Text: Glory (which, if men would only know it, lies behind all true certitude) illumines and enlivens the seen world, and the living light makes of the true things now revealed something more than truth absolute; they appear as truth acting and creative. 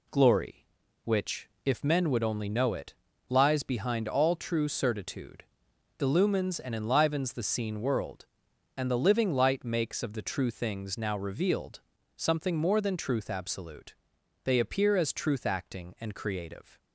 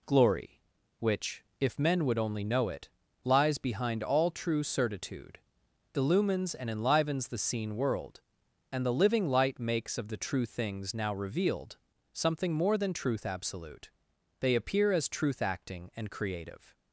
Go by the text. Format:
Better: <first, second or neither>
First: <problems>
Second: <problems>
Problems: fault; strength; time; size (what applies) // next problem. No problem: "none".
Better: neither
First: pauses between "revealed" and "something"; slight; at 11.7 s; 0.36 s long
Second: pauses between "revealed" and "something"; slight; at 11.7 s; 0.36 s long